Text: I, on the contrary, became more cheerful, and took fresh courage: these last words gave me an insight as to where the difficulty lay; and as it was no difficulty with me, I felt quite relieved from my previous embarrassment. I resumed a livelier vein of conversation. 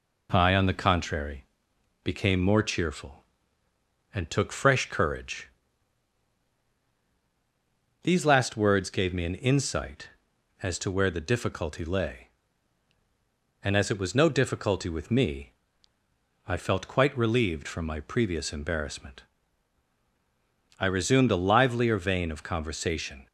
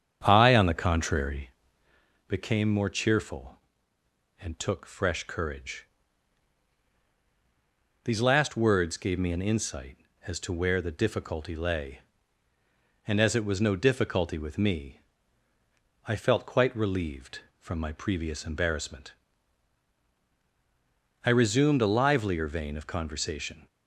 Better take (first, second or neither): first